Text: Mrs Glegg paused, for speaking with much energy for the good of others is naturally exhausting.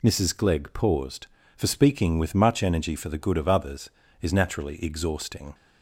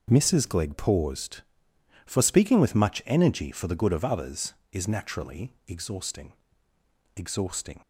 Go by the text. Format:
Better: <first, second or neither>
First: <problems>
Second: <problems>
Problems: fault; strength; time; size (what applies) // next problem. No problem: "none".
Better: first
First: none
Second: says "exhausting" twice; at 7.1 s